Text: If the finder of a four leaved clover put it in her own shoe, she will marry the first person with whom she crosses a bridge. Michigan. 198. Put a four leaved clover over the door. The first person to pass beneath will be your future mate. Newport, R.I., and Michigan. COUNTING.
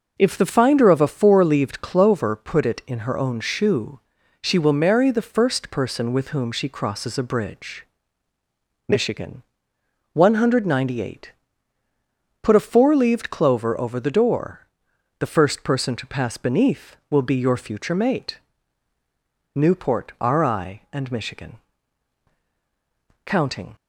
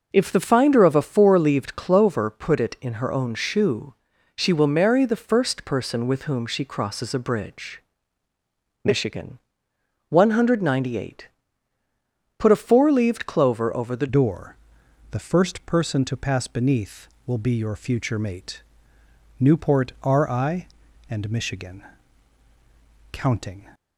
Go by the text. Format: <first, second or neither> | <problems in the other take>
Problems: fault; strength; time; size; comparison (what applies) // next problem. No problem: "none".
first | changes voice at "door"; from 14.0 s on; 9.6 s long